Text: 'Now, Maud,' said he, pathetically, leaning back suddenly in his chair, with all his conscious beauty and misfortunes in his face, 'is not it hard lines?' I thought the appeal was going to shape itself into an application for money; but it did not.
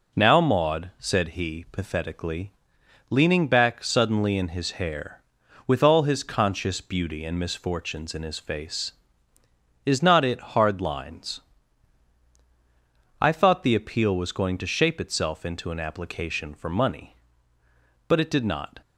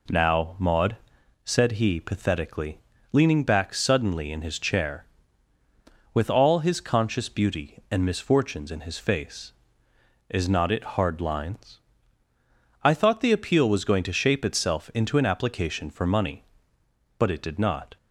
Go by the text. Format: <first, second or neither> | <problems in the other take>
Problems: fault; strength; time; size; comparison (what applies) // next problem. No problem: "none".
second | says "hair" for "chair"; at 4.7 s